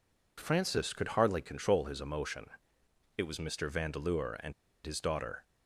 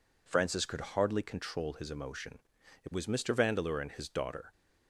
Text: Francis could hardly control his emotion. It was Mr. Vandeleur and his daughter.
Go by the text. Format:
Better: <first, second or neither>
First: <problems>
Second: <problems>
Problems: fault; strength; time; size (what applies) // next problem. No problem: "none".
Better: second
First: pauses between "and" and "his"; slight; at 4.5 s; 0.32 s long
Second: none